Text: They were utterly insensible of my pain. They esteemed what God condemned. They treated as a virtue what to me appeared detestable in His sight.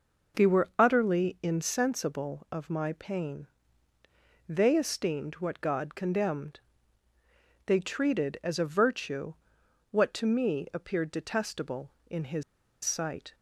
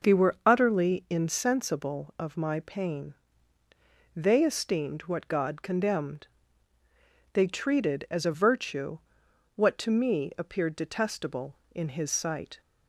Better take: second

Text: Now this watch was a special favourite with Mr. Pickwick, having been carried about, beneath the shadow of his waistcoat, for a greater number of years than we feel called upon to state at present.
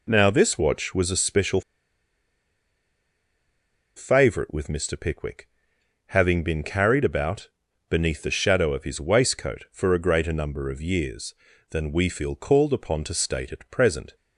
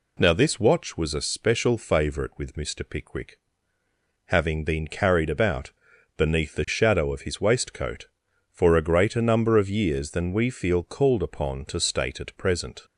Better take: second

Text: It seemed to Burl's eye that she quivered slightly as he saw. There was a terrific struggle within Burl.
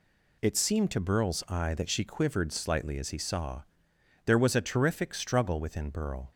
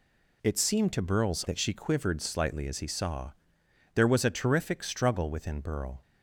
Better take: first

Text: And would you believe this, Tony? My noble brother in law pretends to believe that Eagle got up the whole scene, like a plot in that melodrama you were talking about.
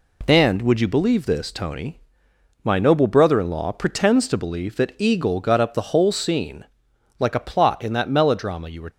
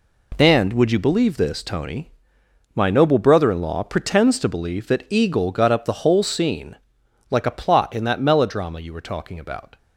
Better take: second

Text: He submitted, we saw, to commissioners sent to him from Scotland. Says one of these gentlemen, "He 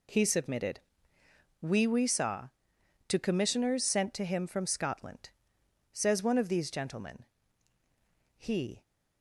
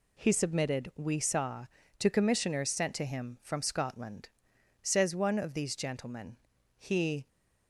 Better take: second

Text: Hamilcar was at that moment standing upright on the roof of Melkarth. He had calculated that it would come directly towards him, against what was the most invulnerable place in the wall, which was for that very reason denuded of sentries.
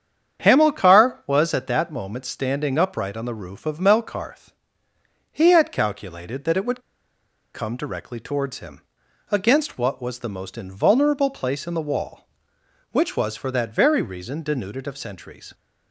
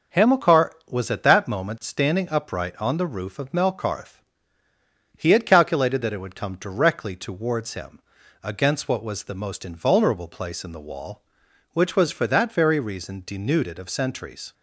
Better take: second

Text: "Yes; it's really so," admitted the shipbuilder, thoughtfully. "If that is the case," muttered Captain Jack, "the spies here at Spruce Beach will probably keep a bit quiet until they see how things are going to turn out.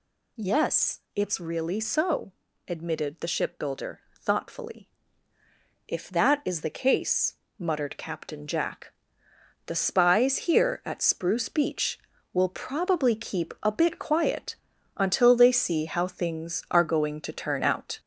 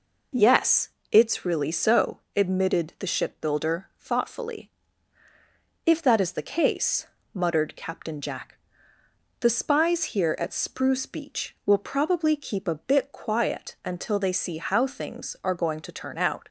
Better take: second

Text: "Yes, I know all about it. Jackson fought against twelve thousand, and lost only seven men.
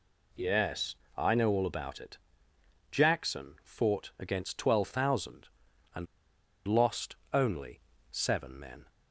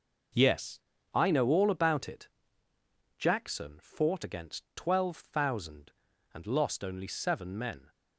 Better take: second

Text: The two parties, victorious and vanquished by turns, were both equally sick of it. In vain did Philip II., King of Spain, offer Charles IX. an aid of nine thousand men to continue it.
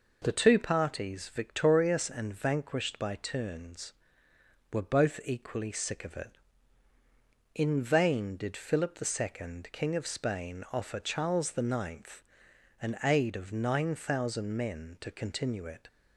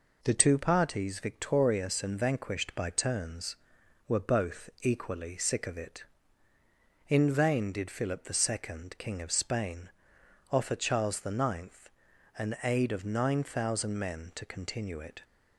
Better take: neither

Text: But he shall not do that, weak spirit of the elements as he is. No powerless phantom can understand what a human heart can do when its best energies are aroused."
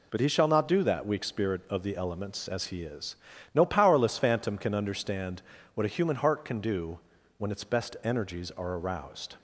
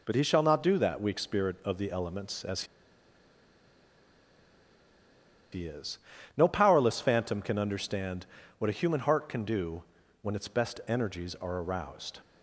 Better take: first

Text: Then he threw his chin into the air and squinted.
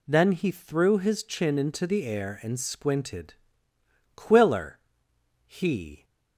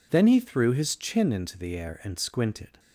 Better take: second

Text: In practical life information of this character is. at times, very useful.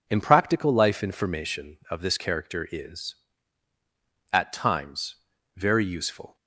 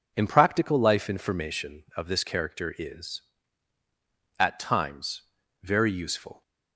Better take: neither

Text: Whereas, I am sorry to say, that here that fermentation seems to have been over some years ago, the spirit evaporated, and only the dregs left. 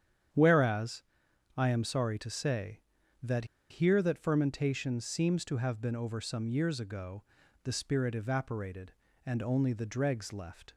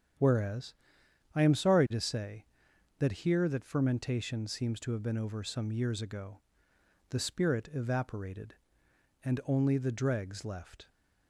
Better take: second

